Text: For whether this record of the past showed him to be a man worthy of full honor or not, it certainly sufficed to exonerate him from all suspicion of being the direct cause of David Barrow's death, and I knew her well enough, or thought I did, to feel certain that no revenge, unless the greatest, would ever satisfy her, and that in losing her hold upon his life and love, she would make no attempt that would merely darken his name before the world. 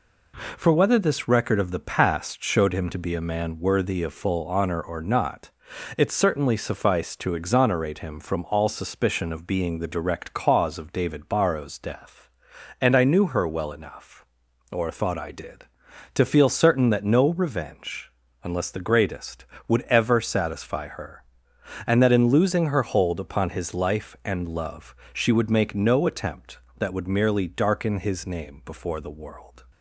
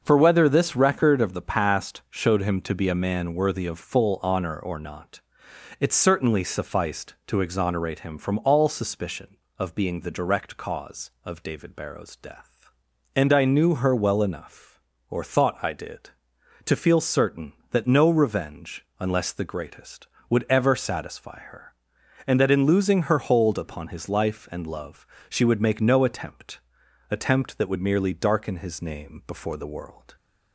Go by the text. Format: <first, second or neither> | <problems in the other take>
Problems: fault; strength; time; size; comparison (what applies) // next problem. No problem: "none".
first | starts louder than the rest; noticeable; until 1.0 s; 6 dB // says "attempt" twice; at 27.0 s